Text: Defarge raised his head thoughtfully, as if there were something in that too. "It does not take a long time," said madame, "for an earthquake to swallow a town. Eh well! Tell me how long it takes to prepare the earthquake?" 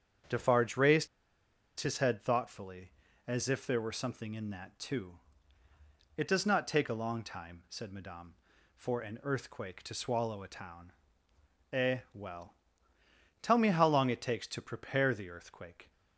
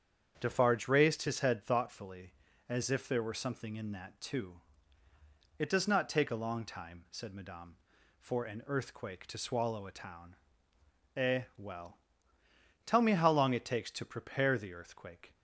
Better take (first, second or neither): second